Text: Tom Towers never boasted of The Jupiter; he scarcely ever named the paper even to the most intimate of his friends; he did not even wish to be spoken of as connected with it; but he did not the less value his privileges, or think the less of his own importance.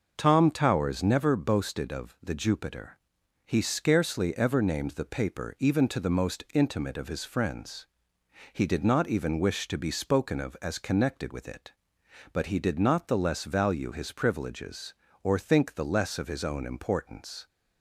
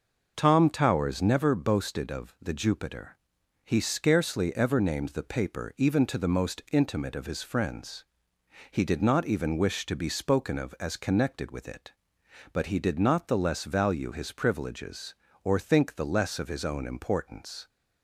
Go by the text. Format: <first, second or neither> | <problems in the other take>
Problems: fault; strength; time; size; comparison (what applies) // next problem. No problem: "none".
neither | none